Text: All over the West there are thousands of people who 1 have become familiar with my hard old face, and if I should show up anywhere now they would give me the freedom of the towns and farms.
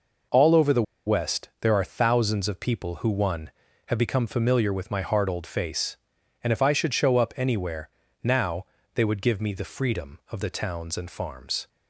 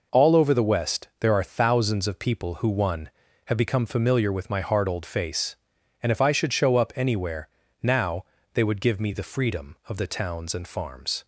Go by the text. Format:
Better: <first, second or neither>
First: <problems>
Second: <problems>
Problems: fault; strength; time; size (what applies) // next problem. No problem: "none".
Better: second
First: pauses between "the" and "West"; slight; at 0.8 s; 0.23 s long // pauses between "anywhere" and "now"; slight; at 7.8 s; 0.34 s long // pauses between "now" and "they"; slight; at 8.6 s; 0.30 s long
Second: pauses between "anywhere" and "now"; slight; at 7.4 s; 0.34 s long // pauses between "now" and "they"; slight; at 8.2 s; 0.30 s long